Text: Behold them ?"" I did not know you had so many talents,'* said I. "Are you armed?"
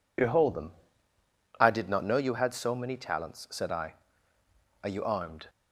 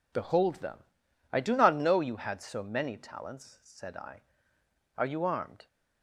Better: first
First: none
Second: says "do" for "did"; at 1.3 s

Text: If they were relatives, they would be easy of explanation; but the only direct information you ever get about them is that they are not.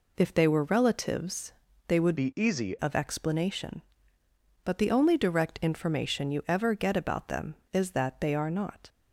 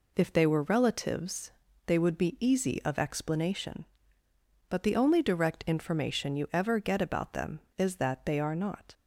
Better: second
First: changes voice from "be" to "easy"; from 2.1 to 2.7 s; 0.6 s long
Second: none

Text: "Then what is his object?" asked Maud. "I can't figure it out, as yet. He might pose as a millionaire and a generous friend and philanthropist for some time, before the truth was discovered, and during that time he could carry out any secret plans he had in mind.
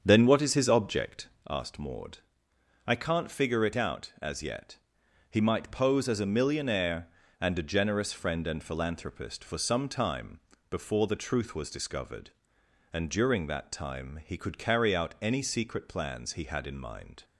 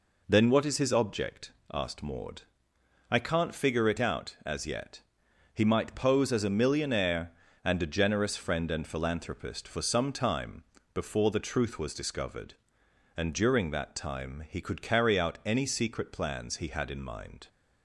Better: second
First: starts louder than the rest; strong; until 1.6 s; 7.5 dB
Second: none

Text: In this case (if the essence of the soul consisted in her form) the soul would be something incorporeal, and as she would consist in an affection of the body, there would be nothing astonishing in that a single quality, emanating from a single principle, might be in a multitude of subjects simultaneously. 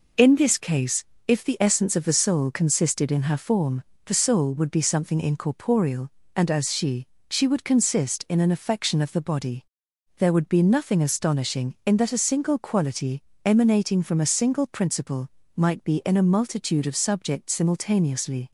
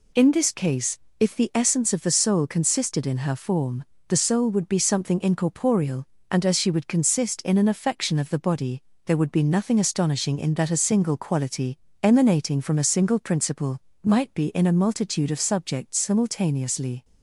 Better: second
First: says "she" twice; at 7.3 s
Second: none

